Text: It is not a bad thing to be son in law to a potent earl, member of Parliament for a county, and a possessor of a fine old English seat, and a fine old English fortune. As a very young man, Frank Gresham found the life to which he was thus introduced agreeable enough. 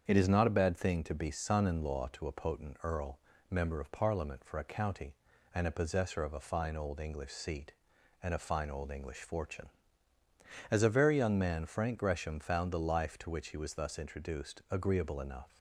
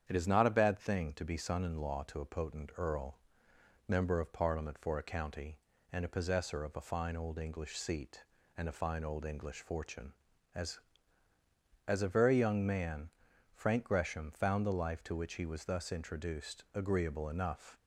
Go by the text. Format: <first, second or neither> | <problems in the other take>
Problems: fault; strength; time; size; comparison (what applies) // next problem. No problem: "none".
first | starts louder than the rest; strong; until 1.0 s; 8.5 dB; strong in the first // says "As" twice; at 11.8 s